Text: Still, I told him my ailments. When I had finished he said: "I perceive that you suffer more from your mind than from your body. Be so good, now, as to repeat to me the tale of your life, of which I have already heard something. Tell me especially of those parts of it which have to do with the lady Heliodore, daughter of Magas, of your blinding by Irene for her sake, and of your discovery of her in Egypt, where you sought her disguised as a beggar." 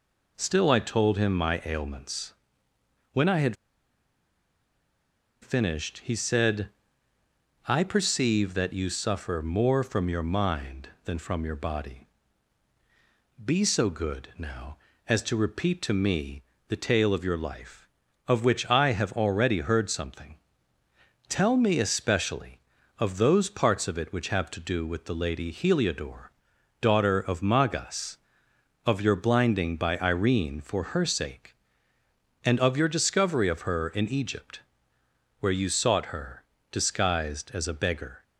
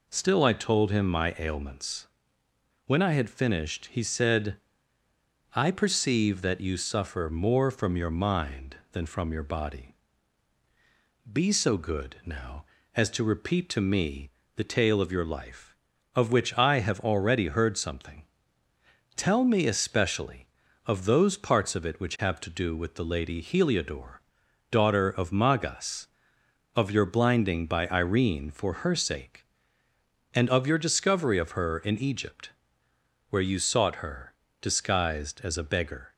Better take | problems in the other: second | pauses between "had" and "finished"; strong; at 3.5 s; 1.8 s long // pauses between "me" and "the"; slight; at 16.4 s; 0.26 s long; slight in the second // pauses between "her" and "disguised"; slight; at 36.4 s; 0.28 s long; slight in the second

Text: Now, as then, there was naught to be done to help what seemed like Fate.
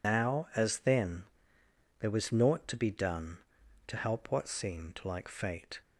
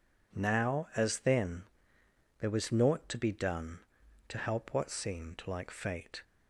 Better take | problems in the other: second | loses the start of "Now"; at 0.0 s; 125 ms

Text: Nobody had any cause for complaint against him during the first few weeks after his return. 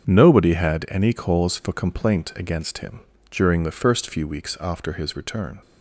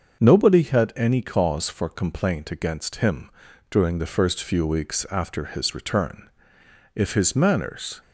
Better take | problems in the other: first | starts louder than the rest; until 1.2 s; 6.5 dB; strong in the first // pauses between "him" and "during"; at 3.3 s; 0.38 s long; slight in the first // goes on to say "If his manners"; noticeable; from 6.9 s on; 1.0 s long

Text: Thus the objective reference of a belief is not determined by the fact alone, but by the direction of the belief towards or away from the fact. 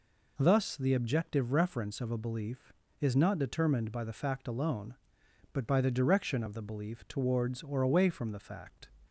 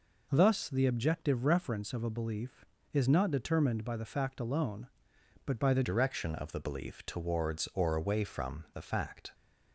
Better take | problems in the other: first | changes voice at "direction"; from 5.8 s on; 3.5 s long

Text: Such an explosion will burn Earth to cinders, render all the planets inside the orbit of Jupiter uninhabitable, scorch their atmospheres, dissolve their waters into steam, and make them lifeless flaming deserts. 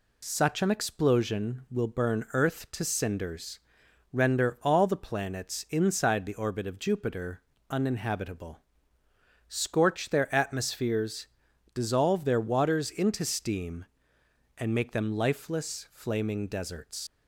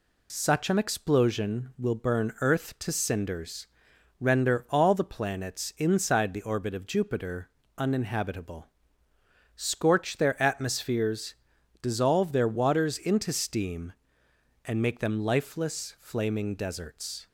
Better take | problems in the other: second | pauses between "Jupiter" and "uninhabitable"; slight; at 7.4 s; 0.28 s long; slight in the second // leaves "deserts" unfinished; at 17.0 s; 125 ms

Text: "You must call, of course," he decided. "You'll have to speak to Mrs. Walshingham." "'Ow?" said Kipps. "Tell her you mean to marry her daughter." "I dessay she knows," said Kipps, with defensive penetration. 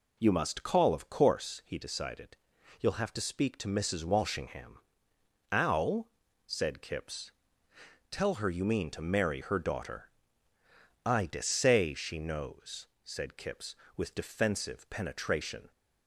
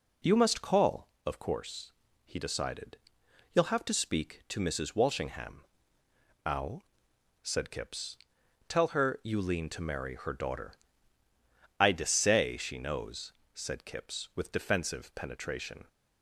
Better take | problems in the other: first | says "lean" for "mean"; at 9.4 s

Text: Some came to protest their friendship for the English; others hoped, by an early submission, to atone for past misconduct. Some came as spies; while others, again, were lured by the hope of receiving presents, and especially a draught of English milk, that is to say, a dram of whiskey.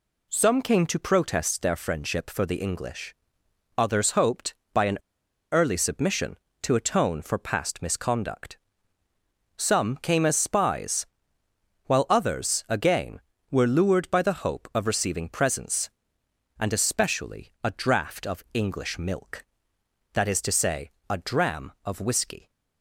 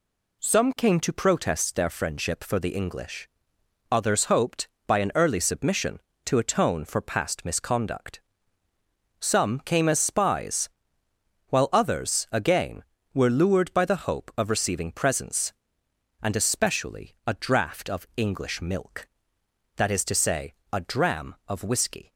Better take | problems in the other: second | pauses between "an" and "early"; noticeable; at 4.9 s; 0.52 s long

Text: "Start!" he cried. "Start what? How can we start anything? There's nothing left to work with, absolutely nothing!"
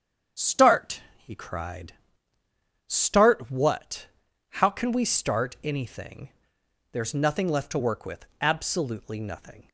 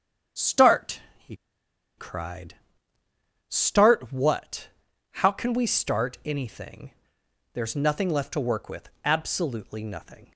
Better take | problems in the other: first | starts louder than the rest; strong; until 2.1 s; 8 dB; strong in the first // pauses between "he" and "cried"; noticeable; at 1.3 s; 0.62 s long

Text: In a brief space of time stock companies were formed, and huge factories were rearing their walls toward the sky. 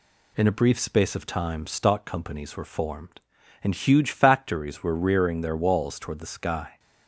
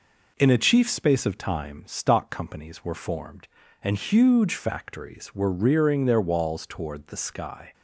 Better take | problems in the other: first | says "chief" for "brief"; at 0.5 s

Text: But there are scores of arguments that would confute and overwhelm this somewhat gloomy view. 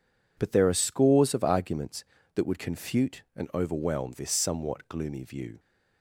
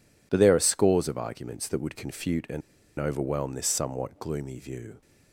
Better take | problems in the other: first | pauses between "and" and "overwhelm"; at 2.6 s; 0.40 s long

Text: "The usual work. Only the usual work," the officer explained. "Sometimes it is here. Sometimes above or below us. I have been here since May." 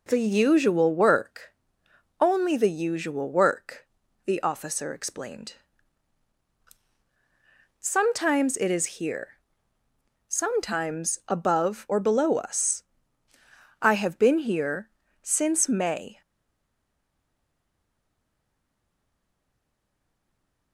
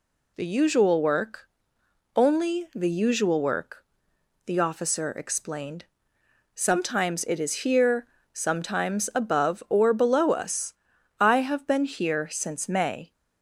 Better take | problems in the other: second | pauses between "here" and "since"; slight; at 14.8 s; 0.34 s long // stays silent after the last word; strong; from 16.2 s on; 4.5 s long

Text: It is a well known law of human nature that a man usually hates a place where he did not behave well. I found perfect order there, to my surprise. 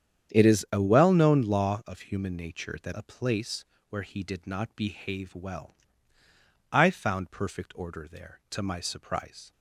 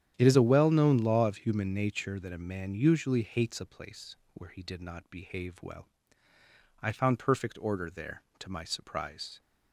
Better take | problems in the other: second | starts louder than the rest; strong; until 1.3 s; 9 dB; strong in the second // skips "a man usually hates"; at 2.9 s // pauses between "place" and "where"; slight; at 3.6 s; 0.24 s long; slight in the second

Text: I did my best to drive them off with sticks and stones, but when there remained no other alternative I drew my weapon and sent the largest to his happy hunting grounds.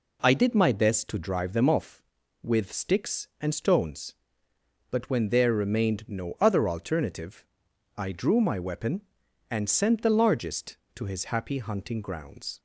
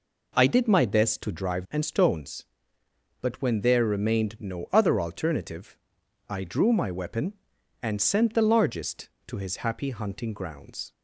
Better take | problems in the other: first | skips "them off with sticks"; at 1.6 s // pauses between "alternative" and "I"; noticeable; at 5.7 s; 0.52 s long; noticeable in the first

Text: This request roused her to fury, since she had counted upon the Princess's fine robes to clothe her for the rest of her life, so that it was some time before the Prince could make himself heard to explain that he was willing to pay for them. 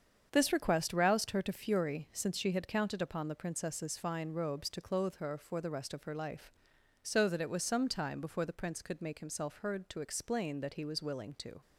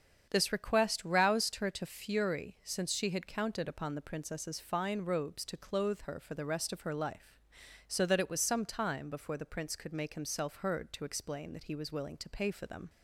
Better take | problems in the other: second | starts louder than the rest; strong; until 1.3 s; 7.5 dB; strong in the second // stops before "pay for them"; at 11.6 s

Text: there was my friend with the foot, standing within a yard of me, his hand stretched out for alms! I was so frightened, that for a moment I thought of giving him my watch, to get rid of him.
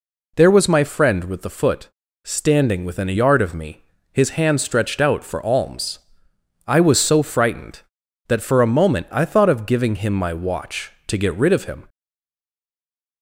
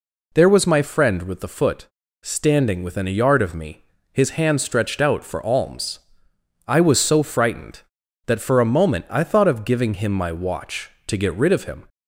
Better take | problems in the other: second | stays silent after the last word; noticeable; from 11.8 s on; 1.4 s long

